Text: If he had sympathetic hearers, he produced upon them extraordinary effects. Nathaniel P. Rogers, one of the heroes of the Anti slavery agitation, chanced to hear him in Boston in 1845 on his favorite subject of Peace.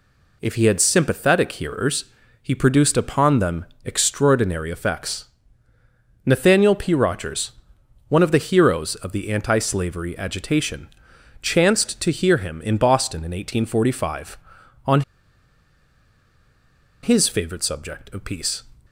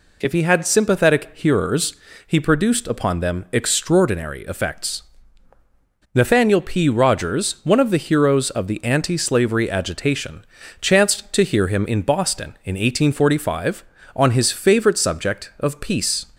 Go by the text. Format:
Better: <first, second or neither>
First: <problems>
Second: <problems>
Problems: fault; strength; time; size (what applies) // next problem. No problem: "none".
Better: second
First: pauses between "them" and "extraordinary"; slight; at 3.6 s; 0.20 s long // pauses between "on" and "his"; strong; at 15.0 s; 2.0 s long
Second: none